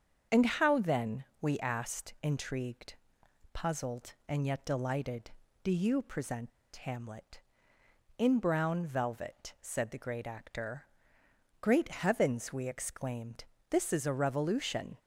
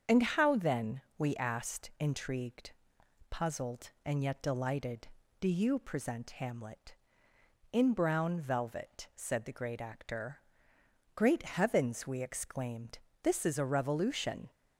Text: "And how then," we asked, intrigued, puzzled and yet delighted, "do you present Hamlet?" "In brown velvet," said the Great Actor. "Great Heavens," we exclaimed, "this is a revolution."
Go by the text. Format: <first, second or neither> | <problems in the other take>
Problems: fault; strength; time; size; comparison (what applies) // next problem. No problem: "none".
second | starts louder than the rest; until 1.5 s; 7 dB; strong in the second // pauses between "present" and "Hamlet"; slight; at 6.5 s; 0.27 s long